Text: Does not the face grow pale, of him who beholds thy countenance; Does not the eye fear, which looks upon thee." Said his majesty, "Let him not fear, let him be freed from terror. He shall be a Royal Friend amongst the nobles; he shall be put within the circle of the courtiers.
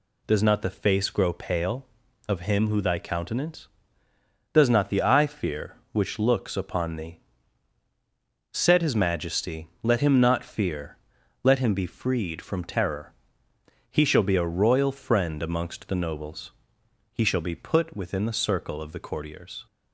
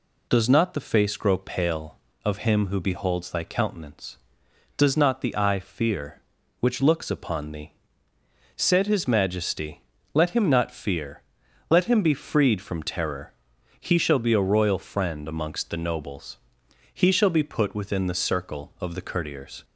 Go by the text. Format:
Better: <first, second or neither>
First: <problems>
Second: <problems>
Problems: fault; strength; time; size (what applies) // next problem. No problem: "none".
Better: second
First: skips "beholds"; at 2.8 s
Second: none